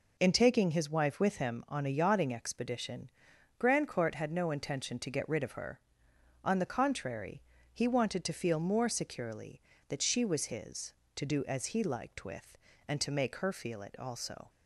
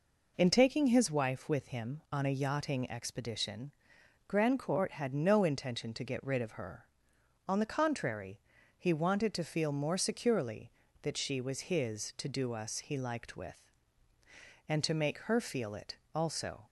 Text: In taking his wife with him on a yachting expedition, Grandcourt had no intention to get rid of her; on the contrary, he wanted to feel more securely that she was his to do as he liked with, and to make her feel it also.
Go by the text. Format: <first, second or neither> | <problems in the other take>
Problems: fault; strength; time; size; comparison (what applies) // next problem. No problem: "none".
first | says "us" for "as"; at 12.5 s // pauses between "it" and "also"; slight; at 15.9 s; 0.18 s long